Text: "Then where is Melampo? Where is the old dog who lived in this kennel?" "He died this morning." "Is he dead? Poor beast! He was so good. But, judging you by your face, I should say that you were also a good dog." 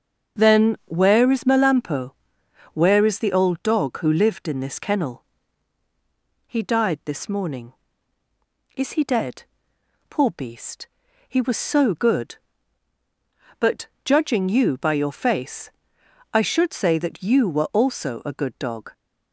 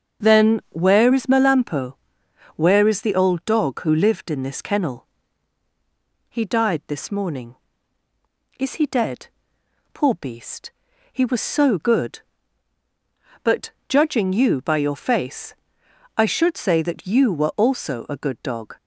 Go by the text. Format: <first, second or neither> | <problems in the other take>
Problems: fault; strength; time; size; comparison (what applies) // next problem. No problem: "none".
neither | starts louder than the rest; the same in both